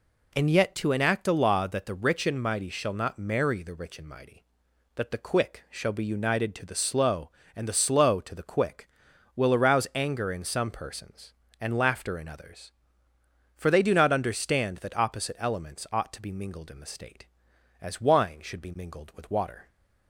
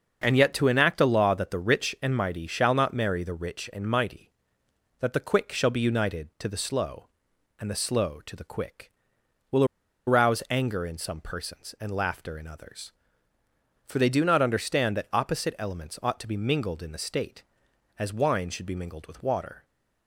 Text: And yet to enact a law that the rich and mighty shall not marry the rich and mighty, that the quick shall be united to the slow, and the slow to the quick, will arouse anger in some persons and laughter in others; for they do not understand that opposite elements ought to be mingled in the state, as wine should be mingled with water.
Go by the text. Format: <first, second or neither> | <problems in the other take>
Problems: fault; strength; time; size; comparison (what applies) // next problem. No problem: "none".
first | starts louder than the rest; until 1.2 s; 6.5 dB // pauses between "will" and "arouse"; at 9.6 s; 0.42 s long